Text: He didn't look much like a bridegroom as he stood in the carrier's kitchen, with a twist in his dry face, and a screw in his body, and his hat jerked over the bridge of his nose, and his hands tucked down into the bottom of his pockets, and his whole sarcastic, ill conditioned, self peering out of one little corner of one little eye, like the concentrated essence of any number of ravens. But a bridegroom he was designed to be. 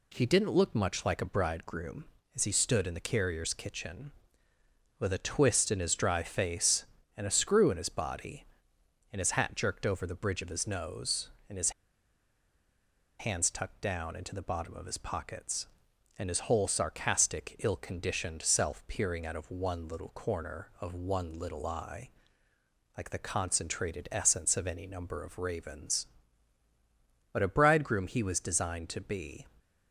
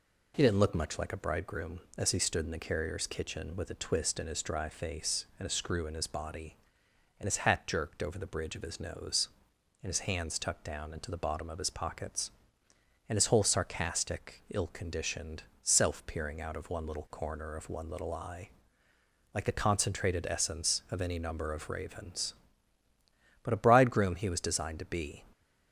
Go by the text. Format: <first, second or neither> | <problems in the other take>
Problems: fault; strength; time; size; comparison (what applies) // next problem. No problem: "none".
second | pauses between "his" and "hands"; strong; at 11.7 s; 1.4 s long